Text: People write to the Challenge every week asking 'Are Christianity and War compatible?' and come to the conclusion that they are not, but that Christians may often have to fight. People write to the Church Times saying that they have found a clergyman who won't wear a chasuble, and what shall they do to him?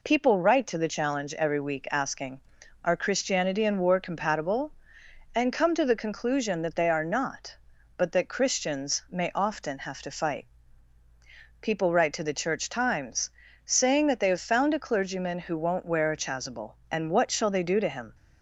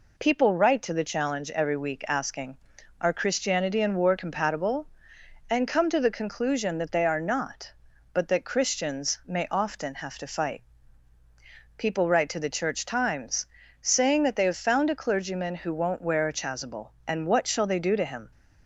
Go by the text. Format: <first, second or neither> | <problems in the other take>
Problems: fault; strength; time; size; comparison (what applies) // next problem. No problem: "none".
neither | pauses between "Times" and "saying"; slight; the same in both